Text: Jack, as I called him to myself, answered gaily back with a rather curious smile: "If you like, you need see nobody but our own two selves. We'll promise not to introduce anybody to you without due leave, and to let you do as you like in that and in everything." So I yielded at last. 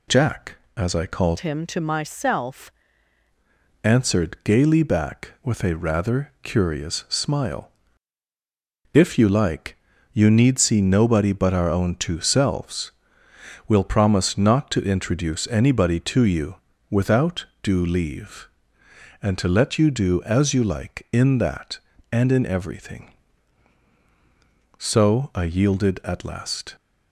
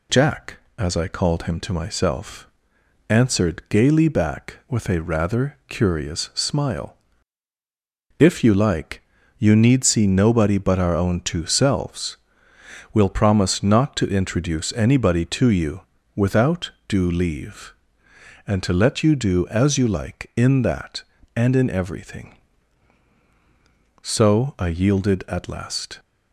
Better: second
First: changes voice from "him" to "myself"; from 1.3 to 2.6 s; 1.3 s long // pauses between "you" and "without"; slight; at 16.5 s; 0.36 s long // pauses between "without" and "due"; slight; at 17.4 s; 0.18 s long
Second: pauses between "you" and "without"; slight; at 15.8 s; 0.36 s long // pauses between "without" and "due"; slight; at 16.7 s; 0.18 s long

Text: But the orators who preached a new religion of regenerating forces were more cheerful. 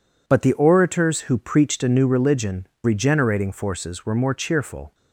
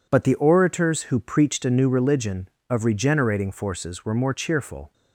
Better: second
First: skips "of"; at 2.7 s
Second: none

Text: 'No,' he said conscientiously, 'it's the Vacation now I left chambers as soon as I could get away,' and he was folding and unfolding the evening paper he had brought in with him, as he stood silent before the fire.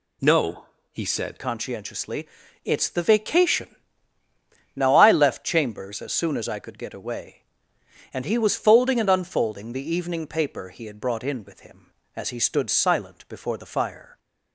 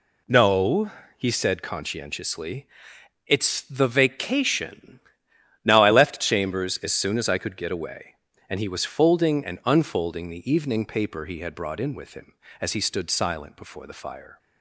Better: second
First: changes voice at "conscientiously"; from 1.3 s on; 12.8 s long // pauses between "Vacation" and "now"; at 3.7 s; 1.0 s long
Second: pauses between "Vacation" and "now"; noticeable; at 4.9 s; 0.66 s long

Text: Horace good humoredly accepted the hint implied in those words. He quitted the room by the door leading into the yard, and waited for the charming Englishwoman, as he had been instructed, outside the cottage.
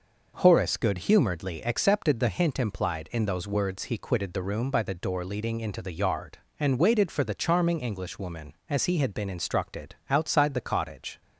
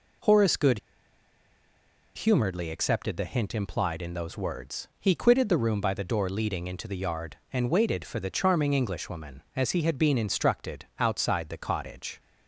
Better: first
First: none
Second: pauses between "good" and "humoredly"; strong; at 0.7 s; 1.3 s long

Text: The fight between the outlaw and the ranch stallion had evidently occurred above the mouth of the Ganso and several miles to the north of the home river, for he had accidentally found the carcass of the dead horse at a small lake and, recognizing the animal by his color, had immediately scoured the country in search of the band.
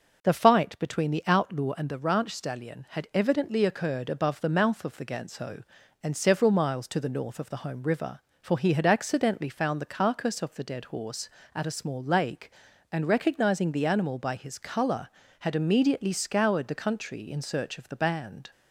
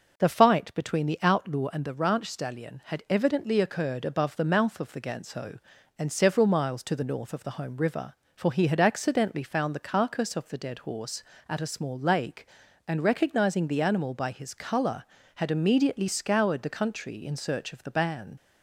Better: first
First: none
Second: leaves "band" unfinished; at 18.3 s; 75 ms

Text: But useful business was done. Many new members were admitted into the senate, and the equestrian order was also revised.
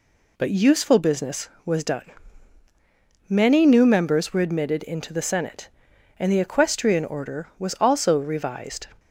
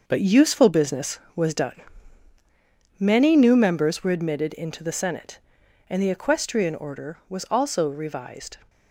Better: first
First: none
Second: gets quieter; strong; throughout; 8.5 dB

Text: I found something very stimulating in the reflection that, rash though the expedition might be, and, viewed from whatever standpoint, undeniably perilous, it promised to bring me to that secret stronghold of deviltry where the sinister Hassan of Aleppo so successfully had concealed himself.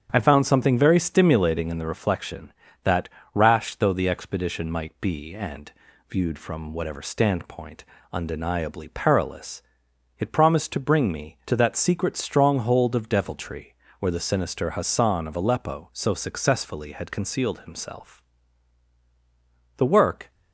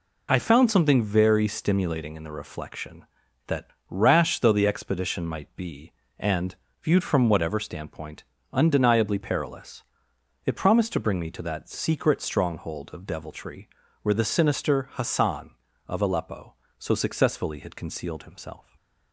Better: second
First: starts louder than the rest; strong; until 1.1 s; 8 dB // pauses between "deviltry" and "where"; slight; at 13.7 s; 0.26 s long // goes on to say "The work"; from 19.7 s on; 0.54 s long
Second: pauses between "deviltry" and "where"; slight; at 13.6 s; 0.36 s long

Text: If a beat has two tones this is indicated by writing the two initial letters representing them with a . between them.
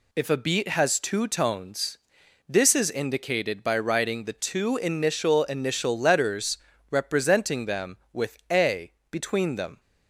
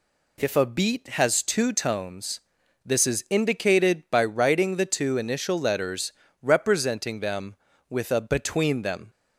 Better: second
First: pauses between "tones" and "this"; noticeable; at 1.9 s; 0.52 s long // says "initial" twice; at 5.4 s // pauses between "letters" and "representing"; slight; at 6.5 s; 0.32 s long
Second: pauses between "tones" and "this"; noticeable; at 2.4 s; 0.46 s long // pauses between "letters" and "representing"; slight; at 6.1 s; 0.28 s long

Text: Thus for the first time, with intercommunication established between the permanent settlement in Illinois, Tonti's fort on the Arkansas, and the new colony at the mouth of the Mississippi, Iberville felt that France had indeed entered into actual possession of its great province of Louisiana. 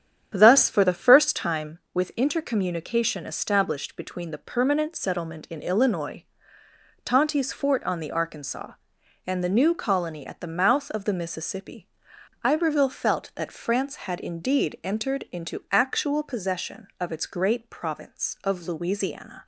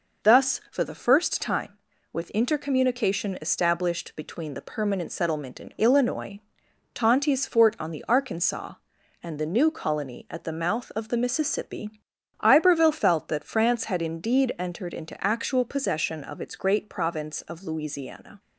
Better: second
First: starts louder than the rest; strong; until 1.6 s; 8.5 dB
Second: none

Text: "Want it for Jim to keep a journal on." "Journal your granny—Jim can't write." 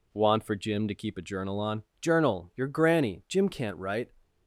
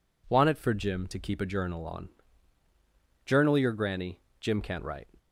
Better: second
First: skips "it"; at 0.4 s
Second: none

